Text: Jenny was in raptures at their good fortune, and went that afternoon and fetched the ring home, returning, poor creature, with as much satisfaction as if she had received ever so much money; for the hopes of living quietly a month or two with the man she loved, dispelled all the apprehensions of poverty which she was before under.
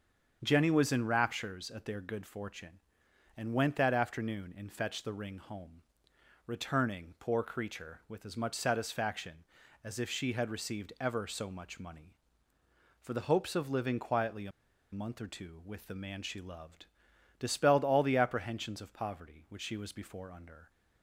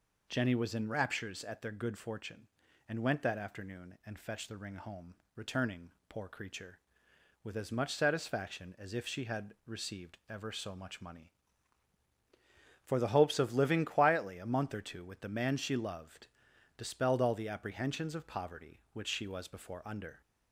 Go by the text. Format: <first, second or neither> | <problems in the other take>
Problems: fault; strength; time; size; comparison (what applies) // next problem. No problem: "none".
second | starts louder than the rest; strong; until 1.4 s; 7.5 dB // pauses between "a" and "month"; at 14.5 s; 0.42 s long